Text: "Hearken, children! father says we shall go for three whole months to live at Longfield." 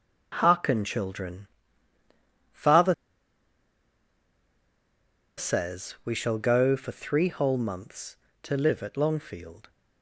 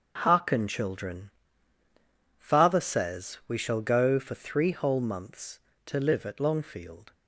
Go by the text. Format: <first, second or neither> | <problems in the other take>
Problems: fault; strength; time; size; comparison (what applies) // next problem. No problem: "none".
second | starts louder than the rest; until 1.3 s; 6 dB; also in the second // pauses between "father" and "says"; strong; at 2.9 s; 2.4 s long